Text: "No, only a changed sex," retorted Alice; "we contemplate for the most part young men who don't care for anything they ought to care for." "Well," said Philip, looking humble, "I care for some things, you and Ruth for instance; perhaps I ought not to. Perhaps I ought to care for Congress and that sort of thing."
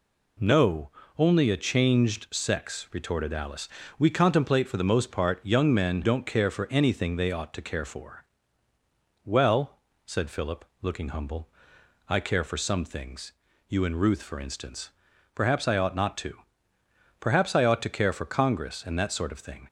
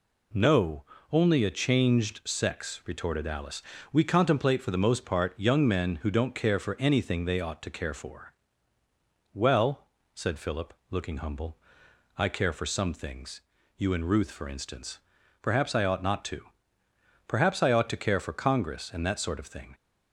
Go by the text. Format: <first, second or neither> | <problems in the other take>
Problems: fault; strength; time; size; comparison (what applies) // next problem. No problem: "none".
second | skips "who"; at 6.0 s